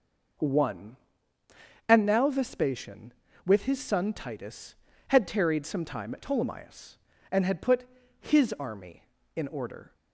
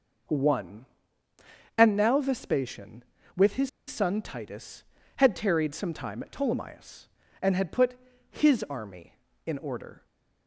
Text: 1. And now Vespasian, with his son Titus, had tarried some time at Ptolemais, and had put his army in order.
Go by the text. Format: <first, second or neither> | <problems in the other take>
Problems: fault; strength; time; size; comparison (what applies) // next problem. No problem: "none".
first | pauses between "his" and "son"; slight; at 3.6 s; 0.18 s long // pauses between "put" and "his"; slight; at 7.9 s; 0.36 s long; slight in the first